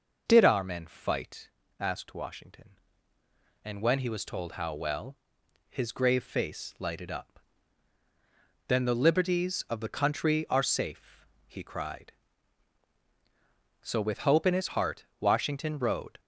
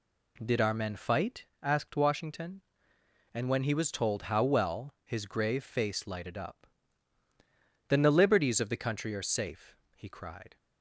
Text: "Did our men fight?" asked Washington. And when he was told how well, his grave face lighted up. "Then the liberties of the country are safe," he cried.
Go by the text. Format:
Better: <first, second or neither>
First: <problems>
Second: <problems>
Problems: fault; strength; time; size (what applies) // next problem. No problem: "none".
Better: second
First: goes on to say "So with hope in his heart Washington rode"; strong; from 13.8 s on; 2.3 s long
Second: none